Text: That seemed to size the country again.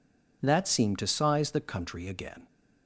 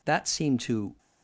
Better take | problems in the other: first | stops before "size the country again"; at 0.9 s

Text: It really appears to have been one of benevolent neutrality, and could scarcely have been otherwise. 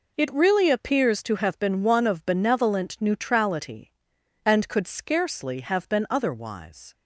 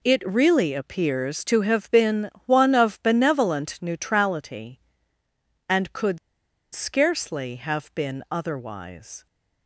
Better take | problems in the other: first | pauses between "been" and "one"; slight; at 2.2 s; 0.16 s long // pauses between "could" and "scarcely"; noticeable; at 6.1 s; 0.55 s long

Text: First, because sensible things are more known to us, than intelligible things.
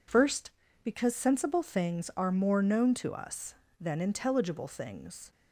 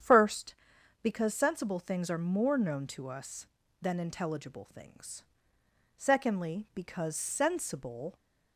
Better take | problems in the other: first | starts louder than the rest; strong; until 1.5 s; 8.5 dB // goes on to say "Secondly because sensible"; strong; from 5.9 s on; 2.1 s long

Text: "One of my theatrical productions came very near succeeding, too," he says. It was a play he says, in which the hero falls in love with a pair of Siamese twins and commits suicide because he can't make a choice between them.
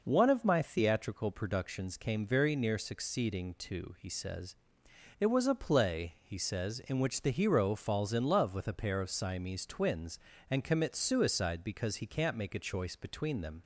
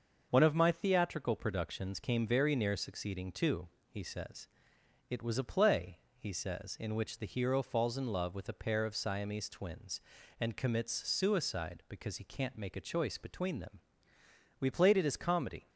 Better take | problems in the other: first | starts louder than the rest; until 1.3 s; 6.5 dB // pauses between "play" and "he"; slight; at 5.9 s; 0.22 s long // goes on to say "We played it as comedy"; noticeable; from 14.5 s on; 1.1 s long

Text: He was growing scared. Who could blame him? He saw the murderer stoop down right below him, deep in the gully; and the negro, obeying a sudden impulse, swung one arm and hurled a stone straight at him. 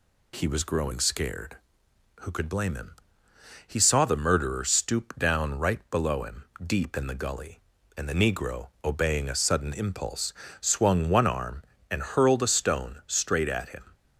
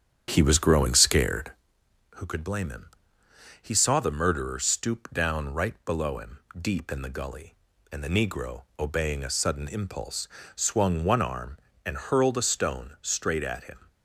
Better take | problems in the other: first | starts louder than the rest; strong; until 1.6 s; 8.5 dB

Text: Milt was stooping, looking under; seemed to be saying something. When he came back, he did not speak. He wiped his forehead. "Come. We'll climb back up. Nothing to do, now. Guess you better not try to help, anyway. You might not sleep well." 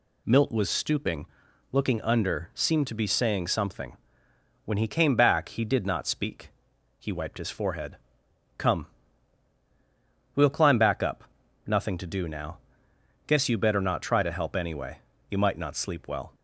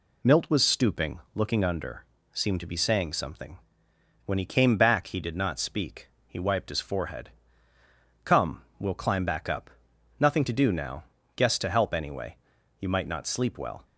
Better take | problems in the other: first | skips "you better not try"; at 11.5 s

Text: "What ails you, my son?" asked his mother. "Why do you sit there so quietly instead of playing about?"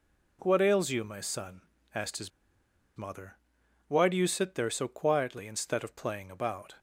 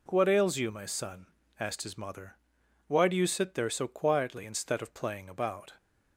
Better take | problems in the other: second | pauses between "his" and "mother"; noticeable; at 2.3 s; 0.67 s long

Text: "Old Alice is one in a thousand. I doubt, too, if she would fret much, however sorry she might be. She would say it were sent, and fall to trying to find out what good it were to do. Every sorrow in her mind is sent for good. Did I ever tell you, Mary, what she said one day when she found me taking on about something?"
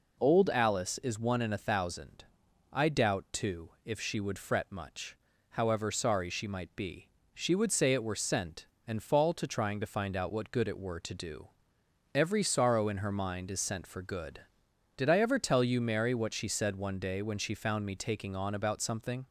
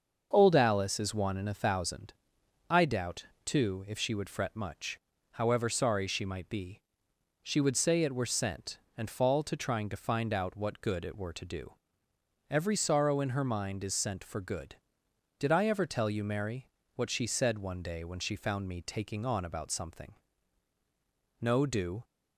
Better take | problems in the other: first | starts louder than the rest; until 1.3 s; 6.5 dB // goes on to say "No do"; noticeable; from 21.4 s on; 0.62 s long

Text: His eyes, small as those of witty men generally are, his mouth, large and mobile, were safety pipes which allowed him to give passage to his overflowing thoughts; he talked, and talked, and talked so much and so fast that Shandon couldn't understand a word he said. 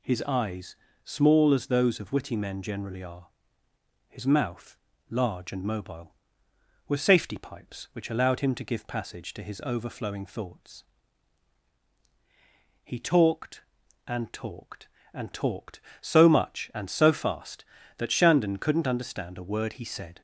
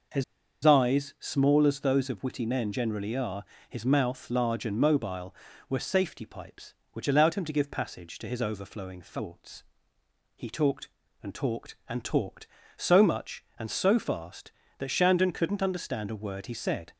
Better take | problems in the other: first | pauses between "His" and "eyes"; at 0.2 s; 0.40 s long

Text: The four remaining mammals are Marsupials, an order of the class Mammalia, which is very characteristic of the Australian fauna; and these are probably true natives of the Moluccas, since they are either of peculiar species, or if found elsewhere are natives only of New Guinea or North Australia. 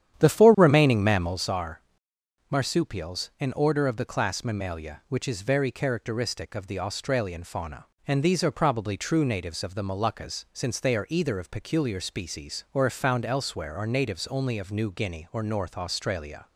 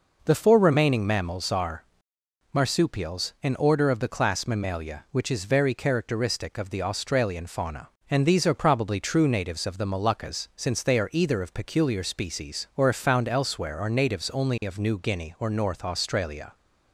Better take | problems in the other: second | starts louder than the rest; strong; until 1.5 s; 10 dB // pauses between "are" and "Marsupials"; noticeable; at 1.7 s; 0.70 s long; noticeable in the second

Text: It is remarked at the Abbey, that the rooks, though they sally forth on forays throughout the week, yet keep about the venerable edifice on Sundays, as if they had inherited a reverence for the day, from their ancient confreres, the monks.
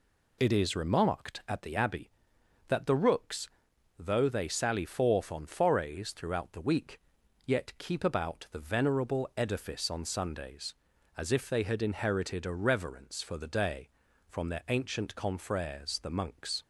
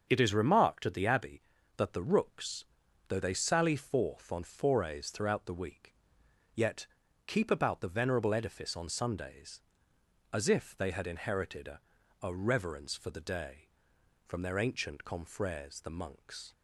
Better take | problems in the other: first | starts louder than the rest; until 1.0 s; 6.5 dB // pauses between "yet" and "keep"; at 6.8 s; 0.40 s long // says "a" twice; at 12.2 s

